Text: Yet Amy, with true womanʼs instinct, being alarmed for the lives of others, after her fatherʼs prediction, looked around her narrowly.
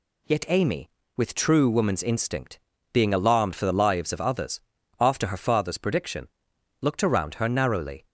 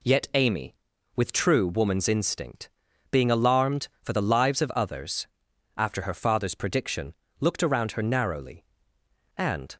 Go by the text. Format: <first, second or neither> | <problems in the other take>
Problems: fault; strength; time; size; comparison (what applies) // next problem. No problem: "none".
first | goes on to say "And"; slight; from 9.3 s on; 0.40 s long